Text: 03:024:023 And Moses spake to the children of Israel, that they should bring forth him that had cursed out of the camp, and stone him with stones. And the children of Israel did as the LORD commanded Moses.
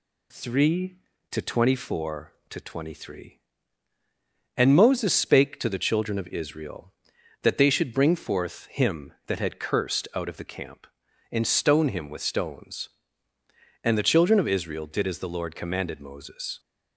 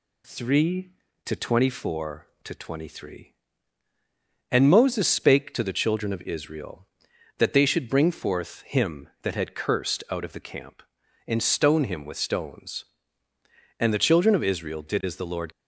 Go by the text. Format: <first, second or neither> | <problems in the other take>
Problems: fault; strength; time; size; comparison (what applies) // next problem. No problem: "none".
first | stops before "commanded Moses"; at 15.5 s